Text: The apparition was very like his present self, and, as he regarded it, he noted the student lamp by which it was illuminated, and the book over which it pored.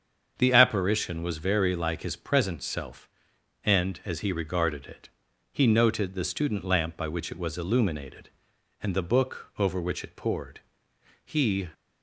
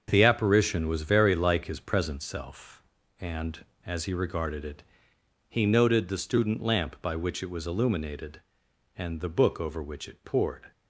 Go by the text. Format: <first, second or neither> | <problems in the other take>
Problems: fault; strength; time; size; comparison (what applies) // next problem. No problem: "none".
second | starts louder than the rest; strong; until 1.3 s; 7 dB; also in the second // goes on to say "He"; slight; from 11.2 s on; 0.44 s long